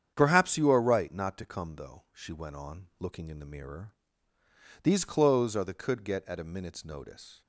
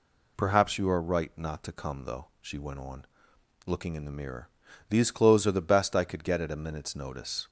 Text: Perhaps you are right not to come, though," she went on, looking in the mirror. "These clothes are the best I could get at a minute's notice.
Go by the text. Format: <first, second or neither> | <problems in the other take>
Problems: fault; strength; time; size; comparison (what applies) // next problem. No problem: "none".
second | starts louder than the rest; strong; until 1.1 s; 8.5 dB // skips "best I"; at 5.7 s